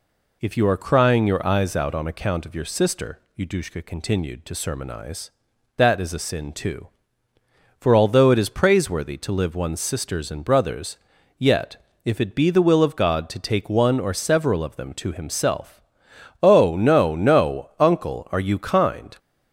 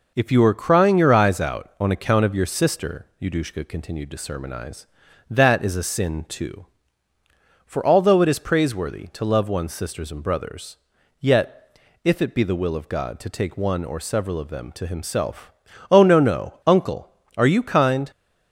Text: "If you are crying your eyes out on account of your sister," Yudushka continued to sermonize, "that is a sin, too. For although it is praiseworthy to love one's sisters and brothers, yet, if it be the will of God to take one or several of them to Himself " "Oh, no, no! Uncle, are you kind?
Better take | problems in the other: second | says "live" for "love"; at 9.3 s

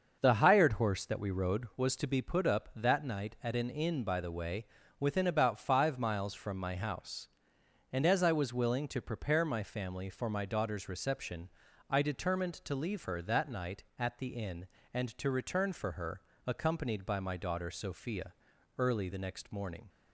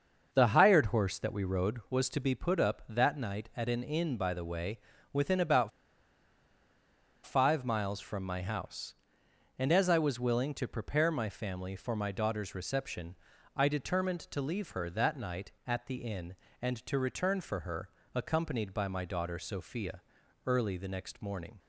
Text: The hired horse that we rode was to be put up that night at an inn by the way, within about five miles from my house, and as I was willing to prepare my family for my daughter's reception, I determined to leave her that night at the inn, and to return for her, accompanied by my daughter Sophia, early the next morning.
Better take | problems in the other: first | starts louder than the rest; until 1.3 s; 6.5 dB; also in the first // pauses between "about" and "five"; strong; at 5.7 s; 1.5 s long

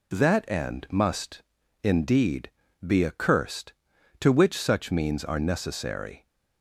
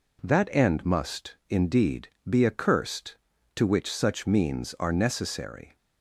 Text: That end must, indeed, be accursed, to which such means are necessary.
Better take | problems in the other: neither | none

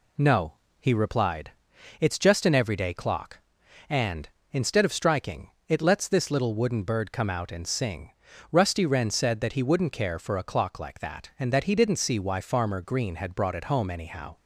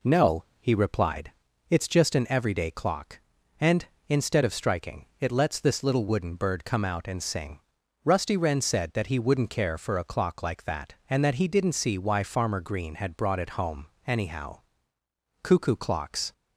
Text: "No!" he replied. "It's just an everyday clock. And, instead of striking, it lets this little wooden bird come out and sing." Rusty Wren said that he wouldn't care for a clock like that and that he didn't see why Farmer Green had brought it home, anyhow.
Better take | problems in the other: first | goes on to say "Cuckoo clocks"; noticeable; from 15.4 s on; 0.90 s long

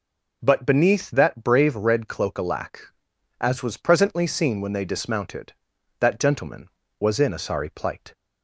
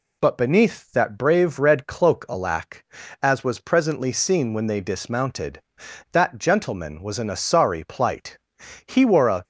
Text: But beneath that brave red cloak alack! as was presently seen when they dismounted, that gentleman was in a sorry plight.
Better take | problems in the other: first | goes on to say "He wore a"; from 8.8 s on; 0.56 s long

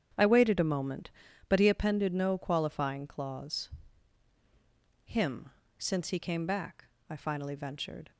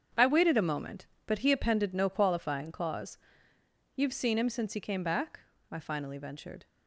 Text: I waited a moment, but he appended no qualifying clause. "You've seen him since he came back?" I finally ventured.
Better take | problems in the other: second | starts louder than the rest; strong; until 1.5 s; 9 dB; strong in the second // skips "You've seen"; at 4.3 s // pauses between "him" and "since"; slight; at 5.5 s; 0.28 s long

